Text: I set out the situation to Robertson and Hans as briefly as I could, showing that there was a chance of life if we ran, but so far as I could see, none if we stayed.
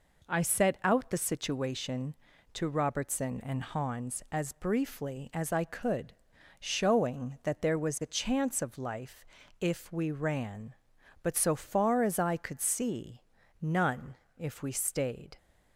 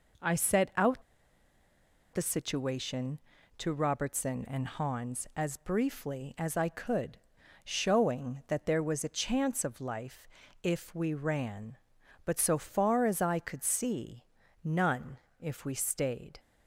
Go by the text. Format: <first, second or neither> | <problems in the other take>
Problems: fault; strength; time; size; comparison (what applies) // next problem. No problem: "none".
first | pauses between "out" and "the"; at 1.0 s; 1.1 s long // pauses between "life" and "if"; slight; at 10.2 s; 0.36 s long; slight in the first // pauses between "none" and "if"; slight; at 15.1 s; 0.22 s long; slight in the first